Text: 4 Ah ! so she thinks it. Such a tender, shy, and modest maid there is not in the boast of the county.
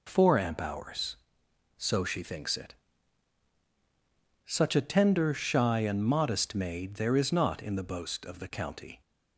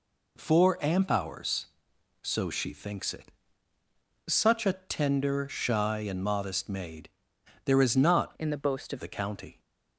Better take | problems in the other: first | pauses between "maid" and "there"; noticeable; at 7.0 s; 0.56 s long // changes voice from "in" to "of"; from 8.3 to 8.9 s; 0.6 s long

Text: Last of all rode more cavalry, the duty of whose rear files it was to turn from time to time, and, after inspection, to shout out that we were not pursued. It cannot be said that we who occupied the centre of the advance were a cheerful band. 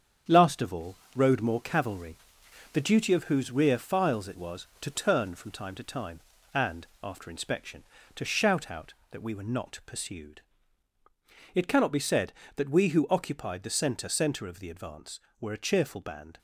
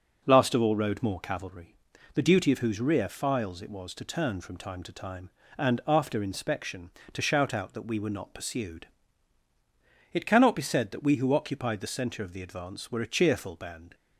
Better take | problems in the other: second | starts louder than the rest; strong; until 1.4 s; 8 dB // pauses between "all" and "rode"; slight; at 0.9 s; 0.18 s long // says "centre" twice; at 14.0 s

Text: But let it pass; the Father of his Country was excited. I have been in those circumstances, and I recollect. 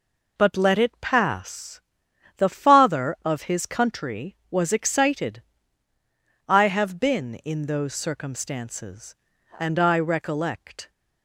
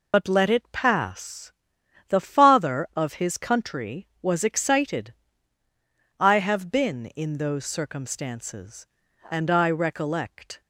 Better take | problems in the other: first | loses the start of "But"; at 0.1 s; 50 ms

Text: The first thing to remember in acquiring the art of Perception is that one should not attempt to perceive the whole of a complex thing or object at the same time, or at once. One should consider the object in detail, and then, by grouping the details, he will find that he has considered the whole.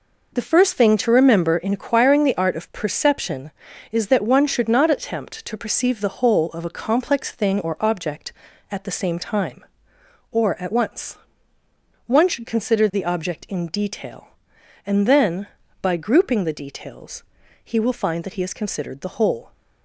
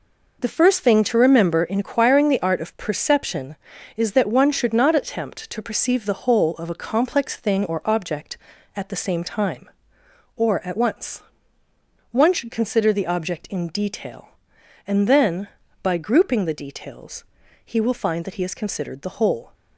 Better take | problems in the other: neither | none

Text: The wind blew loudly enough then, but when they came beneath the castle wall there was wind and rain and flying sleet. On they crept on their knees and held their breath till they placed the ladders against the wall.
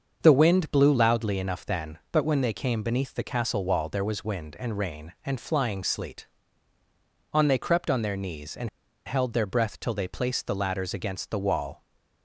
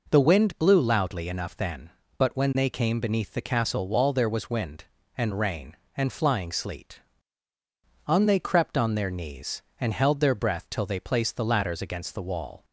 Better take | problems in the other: second | starts louder than the rest; until 1.2 s; 6.5 dB // pauses between "and" and "held"; at 8.6 s; 0.37 s long // stays silent after the last word; slight; from 11.7 s on; 0.5 s long

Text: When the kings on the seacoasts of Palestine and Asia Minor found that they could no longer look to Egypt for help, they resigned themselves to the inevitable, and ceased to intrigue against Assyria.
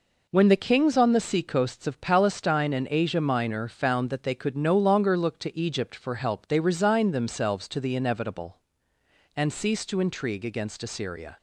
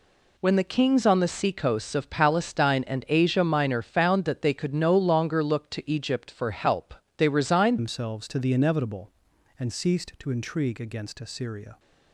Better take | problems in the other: first | changes voice at "themselves"; from 7.7 s on; 4.0 s long

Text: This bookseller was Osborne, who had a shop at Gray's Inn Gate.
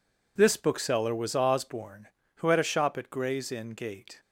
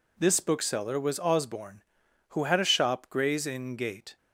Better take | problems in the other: first | skips "at"; at 3.0 s

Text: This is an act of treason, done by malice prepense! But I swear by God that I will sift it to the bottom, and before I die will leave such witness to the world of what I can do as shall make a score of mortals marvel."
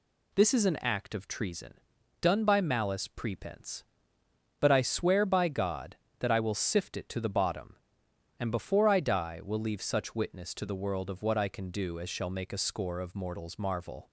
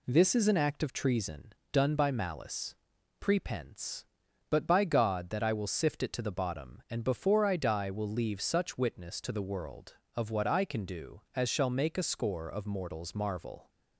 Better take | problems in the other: first | pauses between "malice" and "prepense"; noticeable; at 2.7 s; 0.48 s long // skips "I swear"; at 4.6 s

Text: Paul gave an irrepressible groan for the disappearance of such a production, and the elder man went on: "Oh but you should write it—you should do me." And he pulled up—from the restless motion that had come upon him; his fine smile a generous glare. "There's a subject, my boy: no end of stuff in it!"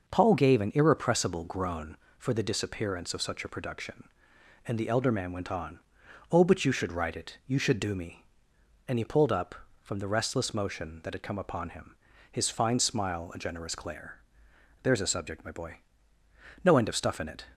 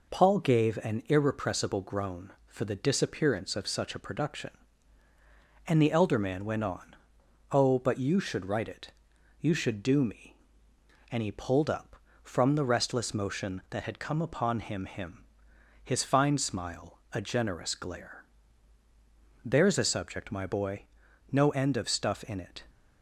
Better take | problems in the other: first | says "him" twice; at 14.8 s // pauses between "smile" and "a"; slight; at 16.9 s; 0.16 s long

